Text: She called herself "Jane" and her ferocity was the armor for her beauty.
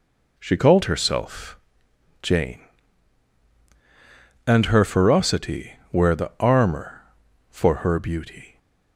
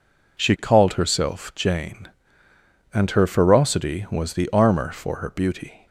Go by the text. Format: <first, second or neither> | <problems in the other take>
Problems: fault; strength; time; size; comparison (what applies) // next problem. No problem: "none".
second | pauses between "herself" and "Jane"; noticeable; at 1.5 s; 0.64 s long // says "were" for "was"; at 5.9 s